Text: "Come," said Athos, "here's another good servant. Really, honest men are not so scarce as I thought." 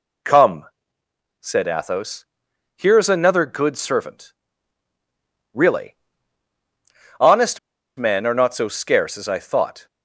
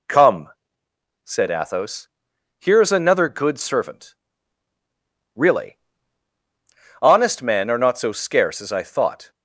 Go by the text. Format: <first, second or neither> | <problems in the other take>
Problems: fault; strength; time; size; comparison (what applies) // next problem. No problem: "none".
second | pauses between "honest" and "men"; at 7.5 s; 0.38 s long